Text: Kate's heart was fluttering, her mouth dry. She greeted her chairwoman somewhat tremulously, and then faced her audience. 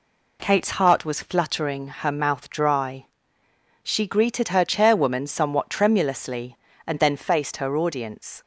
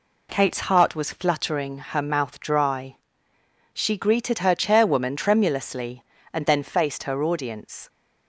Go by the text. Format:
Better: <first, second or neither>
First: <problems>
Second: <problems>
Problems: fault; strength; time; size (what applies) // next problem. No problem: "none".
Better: first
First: none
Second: skips "somewhat"; at 5.1 s